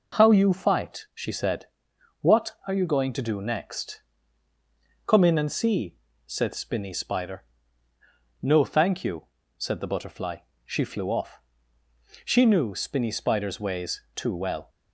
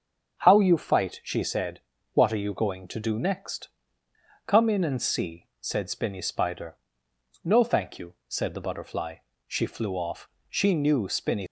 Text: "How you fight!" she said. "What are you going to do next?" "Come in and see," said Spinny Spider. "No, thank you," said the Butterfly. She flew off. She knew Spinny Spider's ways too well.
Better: first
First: none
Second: starts louder than the rest; until 1.4 s; 6.5 dB // stops before "Spider's ways too well"; at 11.4 s

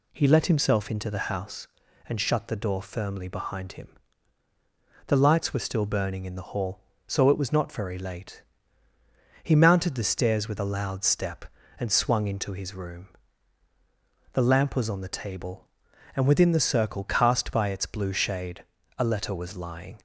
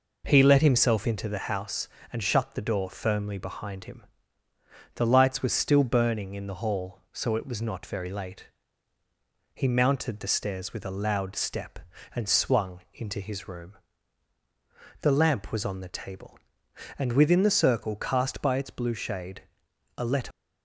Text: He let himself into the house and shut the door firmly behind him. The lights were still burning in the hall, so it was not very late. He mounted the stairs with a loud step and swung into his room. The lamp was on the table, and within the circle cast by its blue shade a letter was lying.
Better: first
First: pauses between "shade" and "a"; slight; at 18.6 s; 0.34 s long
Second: pauses between "shade" and "a"; noticeable; at 19.4 s; 0.54 s long // stops before "was lying"; at 20.3 s

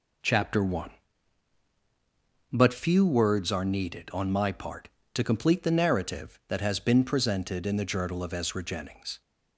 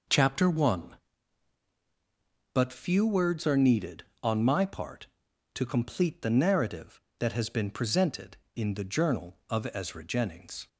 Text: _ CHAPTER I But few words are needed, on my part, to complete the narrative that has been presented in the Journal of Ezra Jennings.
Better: neither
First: none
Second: none

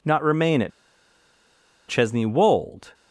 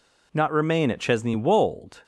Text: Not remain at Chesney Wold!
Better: second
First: pauses between "at" and "Chesney"; at 0.7 s; 1.1 s long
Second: none

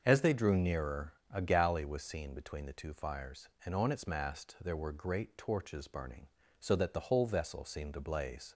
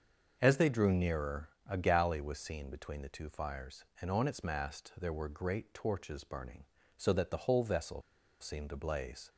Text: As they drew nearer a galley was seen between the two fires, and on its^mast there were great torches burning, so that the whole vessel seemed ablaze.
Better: first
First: starts louder than the rest; until 1.0 s; 6.5 dB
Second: starts louder than the rest; until 1.4 s; 6.5 dB // pauses between "vessel" and "seemed"; at 8.0 s; 0.39 s long

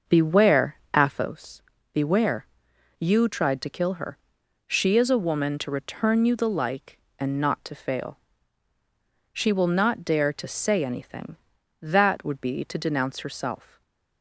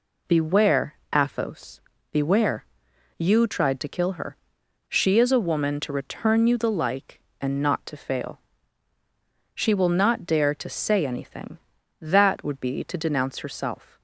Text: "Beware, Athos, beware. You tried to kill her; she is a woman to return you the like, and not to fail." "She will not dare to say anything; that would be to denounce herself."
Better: second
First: starts louder than the rest; noticeable; until 1.3 s; 6 dB // stays silent after the last word; slight; from 13.6 s on; 0.6 s long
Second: none

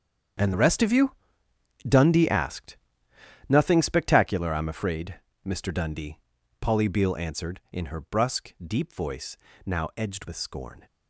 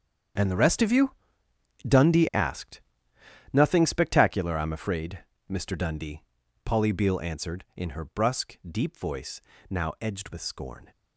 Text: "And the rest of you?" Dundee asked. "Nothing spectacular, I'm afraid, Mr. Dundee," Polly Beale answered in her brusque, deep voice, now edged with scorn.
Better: neither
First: starts louder than the rest; strong; until 2.1 s; 8 dB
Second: starts louder than the rest; strong; until 2.1 s; 8 dB

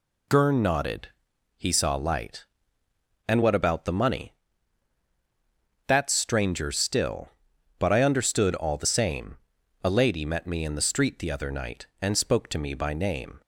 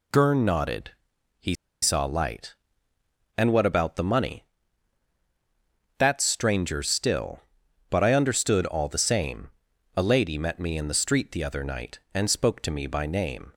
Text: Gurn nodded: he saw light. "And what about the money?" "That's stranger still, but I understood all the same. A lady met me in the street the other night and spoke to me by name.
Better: first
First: none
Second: pauses between "he" and "saw"; slight; at 1.5 s; 0.29 s long

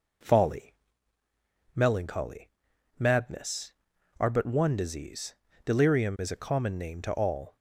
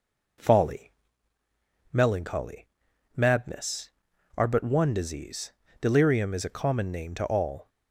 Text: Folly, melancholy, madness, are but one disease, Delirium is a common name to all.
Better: neither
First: none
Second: none

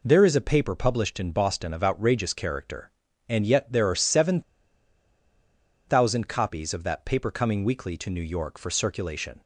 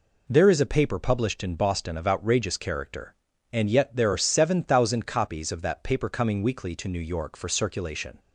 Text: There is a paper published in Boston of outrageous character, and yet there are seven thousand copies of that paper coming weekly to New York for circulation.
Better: second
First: pauses between "seven" and "thousand"; strong; at 4.4 s; 1.4 s long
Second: none

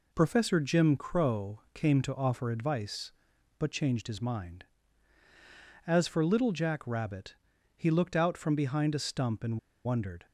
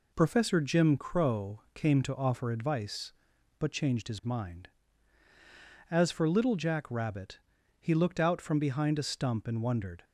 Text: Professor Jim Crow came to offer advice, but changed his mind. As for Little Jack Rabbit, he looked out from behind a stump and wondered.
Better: second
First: pauses between "and" and "wondered"; slight; at 9.5 s; 0.27 s long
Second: none

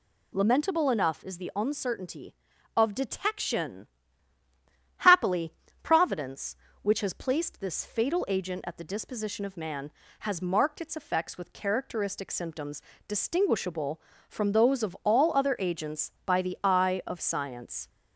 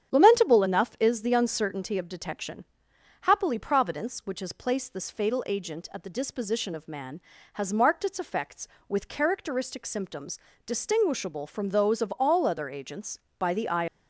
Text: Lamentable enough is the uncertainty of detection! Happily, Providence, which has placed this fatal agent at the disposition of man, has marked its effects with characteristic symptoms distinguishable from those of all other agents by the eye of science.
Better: first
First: pauses between "symptoms" and "distinguishable"; slight; at 12.8 s; 0.26 s long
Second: starts louder than the rest; strong; until 1.1 s; 8.5 dB // pauses between "symptoms" and "distinguishable"; slight; at 10.3 s; 0.26 s long // stops before "of science"; at 13.8 s

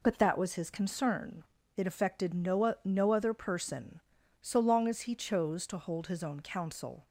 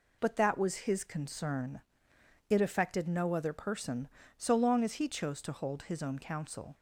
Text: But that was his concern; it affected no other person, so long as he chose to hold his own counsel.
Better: second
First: says "no" twice; at 2.8 s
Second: none

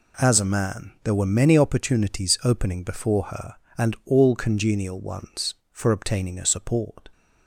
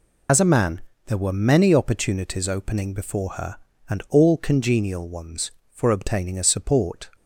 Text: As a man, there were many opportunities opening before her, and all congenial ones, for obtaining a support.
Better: first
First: none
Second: loses the start of "As"; at 0.2 s; 75 ms

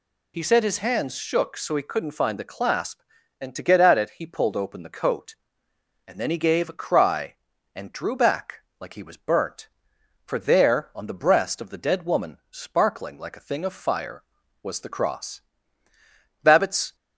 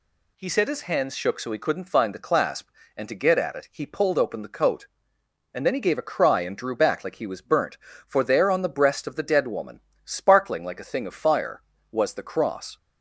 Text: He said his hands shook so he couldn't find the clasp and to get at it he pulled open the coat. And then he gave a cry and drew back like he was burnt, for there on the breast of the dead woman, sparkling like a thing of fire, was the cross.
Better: second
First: pauses between "back" and "like"; slight; at 8.5 s; 0.22 s long // goes on to say "Babbitts"; from 16.4 s on; 0.52 s long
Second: none

